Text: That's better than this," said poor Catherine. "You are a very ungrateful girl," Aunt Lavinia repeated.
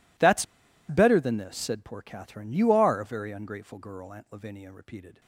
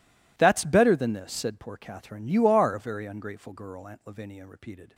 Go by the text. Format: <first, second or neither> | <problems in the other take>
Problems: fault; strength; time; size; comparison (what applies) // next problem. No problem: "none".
second | pauses between "That's" and "better"; at 0.4 s; 0.45 s long